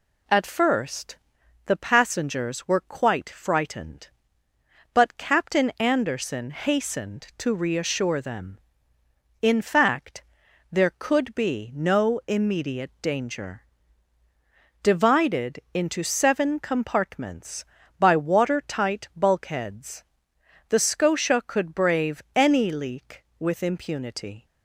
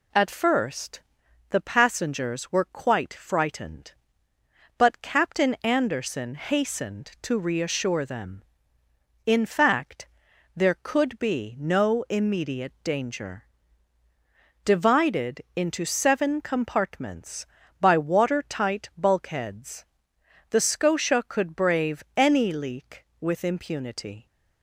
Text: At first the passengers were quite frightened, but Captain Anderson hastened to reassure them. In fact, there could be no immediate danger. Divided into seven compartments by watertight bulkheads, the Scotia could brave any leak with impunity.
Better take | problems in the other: neither | pauses between "first" and "the"; noticeable; the same in both // pauses between "Divided" and "into"; slight; the same in both

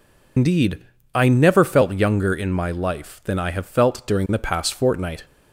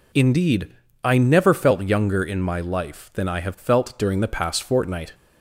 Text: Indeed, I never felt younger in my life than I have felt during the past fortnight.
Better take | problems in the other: second | loses the start of "Indeed"; at 0.3 s; 120 ms

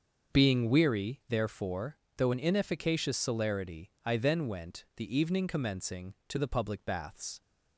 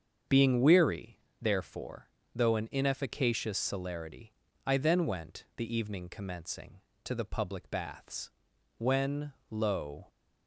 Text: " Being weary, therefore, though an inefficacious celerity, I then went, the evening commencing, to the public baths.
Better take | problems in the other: first | starts louder than the rest; until 1.4 s; 7 dB; also in the first // goes on to say "When lo"; noticeable; from 8.7 s on; 1.3 s long

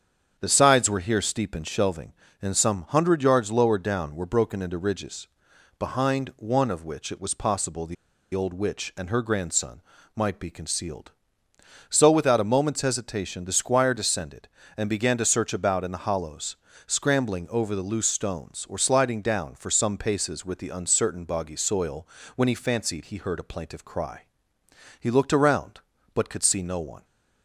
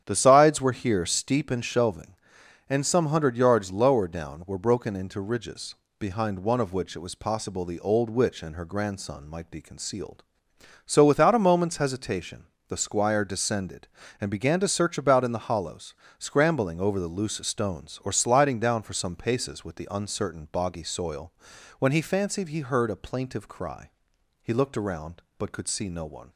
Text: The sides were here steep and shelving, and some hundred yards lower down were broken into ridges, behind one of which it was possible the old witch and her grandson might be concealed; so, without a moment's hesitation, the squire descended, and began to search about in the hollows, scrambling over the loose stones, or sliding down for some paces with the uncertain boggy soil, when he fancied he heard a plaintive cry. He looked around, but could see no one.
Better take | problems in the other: second | starts louder than the rest; strong; until 1.4 s; 8 dB; strong in the second // pauses between "the" and "old"; at 7.9 s; 0.38 s long // pauses between "grandson" and "might"; slight; at 9.8 s; 0.34 s long

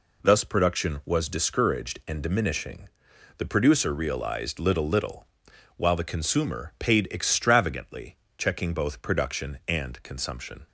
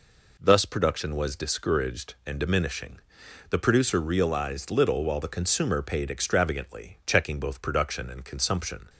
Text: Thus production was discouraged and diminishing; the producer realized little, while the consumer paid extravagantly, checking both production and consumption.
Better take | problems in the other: second | says "little" twice; at 4.8 s

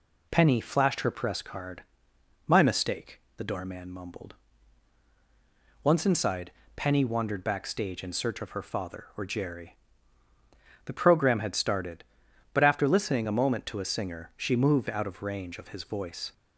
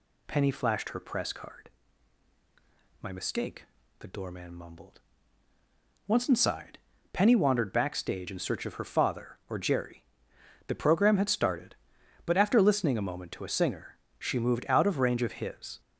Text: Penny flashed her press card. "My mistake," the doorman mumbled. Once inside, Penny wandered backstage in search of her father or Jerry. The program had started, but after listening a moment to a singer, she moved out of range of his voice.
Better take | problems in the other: first | stops before "voice"; at 15.8 s

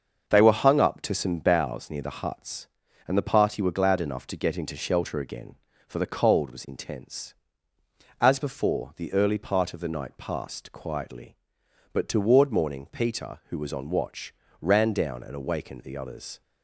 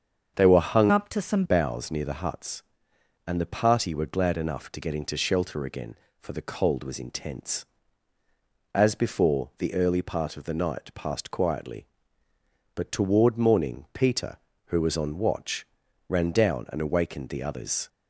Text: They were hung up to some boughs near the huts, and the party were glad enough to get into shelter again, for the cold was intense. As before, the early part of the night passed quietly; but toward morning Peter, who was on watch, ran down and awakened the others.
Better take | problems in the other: first | starts louder than the rest; strong; until 1.3 s; 7 dB; also in the first // changes voice from "up" to "some"; from 0.8 to 1.4 s; 0.6 s long

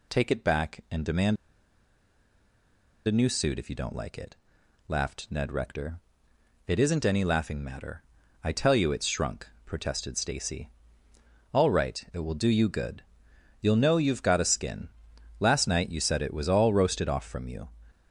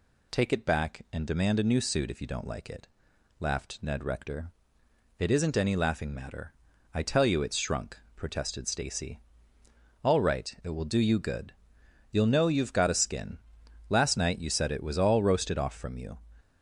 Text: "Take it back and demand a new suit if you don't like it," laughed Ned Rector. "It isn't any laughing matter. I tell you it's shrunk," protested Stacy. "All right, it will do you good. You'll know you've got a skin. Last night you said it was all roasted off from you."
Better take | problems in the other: second | pauses between "demand" and "a"; strong; at 1.3 s; 1.7 s long

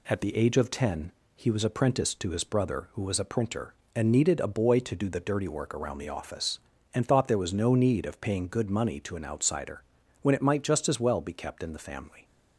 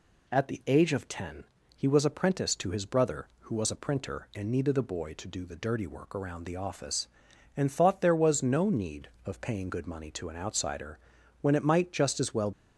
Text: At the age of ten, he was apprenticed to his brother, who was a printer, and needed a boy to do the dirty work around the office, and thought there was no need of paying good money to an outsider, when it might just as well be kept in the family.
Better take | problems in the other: first | stops before "be kept in the family"; at 12.5 s

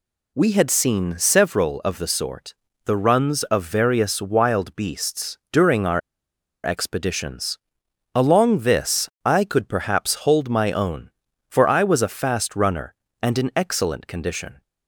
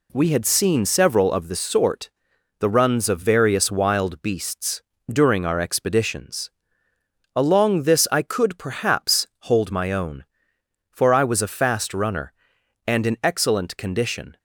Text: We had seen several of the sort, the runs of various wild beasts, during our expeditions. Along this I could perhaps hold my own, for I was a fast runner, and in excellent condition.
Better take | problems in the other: second | pauses between "our" and "expeditions"; noticeable; at 6.0 s; 0.63 s long // pauses between "this" and "I"; slight; at 9.0 s; 0.16 s long

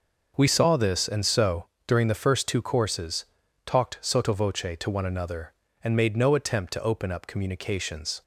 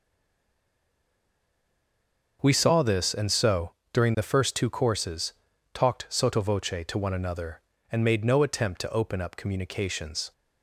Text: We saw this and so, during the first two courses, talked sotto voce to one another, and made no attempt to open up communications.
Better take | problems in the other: first | stays silent before the first word; until 2.4 s; 2.4 s long

